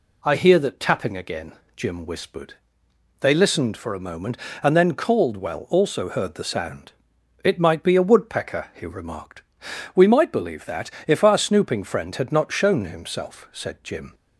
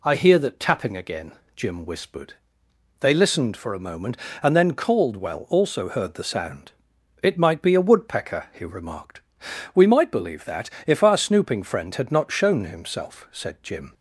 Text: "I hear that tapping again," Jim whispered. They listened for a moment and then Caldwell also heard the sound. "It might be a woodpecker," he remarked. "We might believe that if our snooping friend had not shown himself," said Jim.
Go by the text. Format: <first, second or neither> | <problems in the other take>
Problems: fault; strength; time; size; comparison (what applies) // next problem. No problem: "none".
neither | pauses between "that" and "if"; slight; the same in both